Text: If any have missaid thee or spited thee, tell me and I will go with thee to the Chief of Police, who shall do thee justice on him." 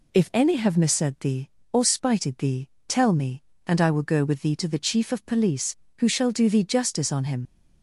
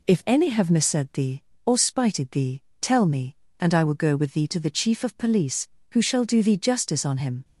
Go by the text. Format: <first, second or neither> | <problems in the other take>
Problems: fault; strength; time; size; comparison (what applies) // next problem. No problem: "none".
second | leaves "him" unfinished; at 7.4 s; 55 ms